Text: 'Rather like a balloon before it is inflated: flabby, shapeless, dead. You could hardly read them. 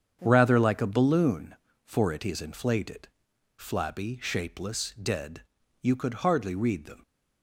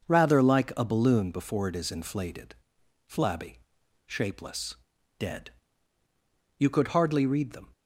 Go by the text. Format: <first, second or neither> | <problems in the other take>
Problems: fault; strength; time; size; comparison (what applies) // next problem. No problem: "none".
second | starts louder than the rest; strong; until 1.2 s; 7.5 dB; noticeable in the second // says "for" for "before"; at 1.8 s